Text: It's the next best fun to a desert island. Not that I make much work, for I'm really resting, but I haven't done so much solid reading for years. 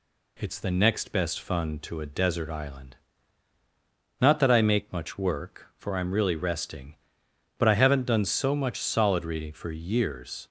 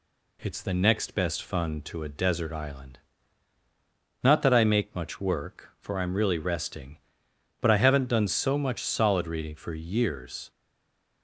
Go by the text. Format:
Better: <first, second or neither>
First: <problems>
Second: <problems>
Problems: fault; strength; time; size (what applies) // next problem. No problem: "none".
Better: first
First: none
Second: stays silent after the last word; slight; from 10.5 s on; 0.7 s long